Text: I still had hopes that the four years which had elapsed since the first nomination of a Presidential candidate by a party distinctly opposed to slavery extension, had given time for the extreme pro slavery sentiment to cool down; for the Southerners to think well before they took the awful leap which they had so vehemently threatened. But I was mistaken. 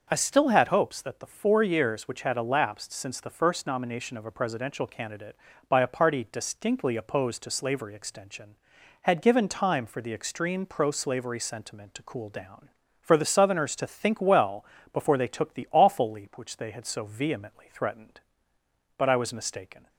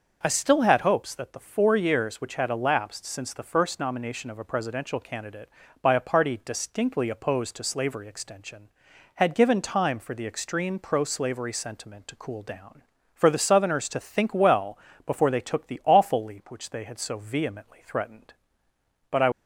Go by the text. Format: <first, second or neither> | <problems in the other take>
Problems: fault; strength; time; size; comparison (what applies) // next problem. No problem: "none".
first | starts louder than the rest; until 1.2 s; 6 dB; also in the first // pauses between "well" and "before"; slight; at 14.7 s; 0.28 s long; slight in the first // stops before "was mistaken"; at 19.3 s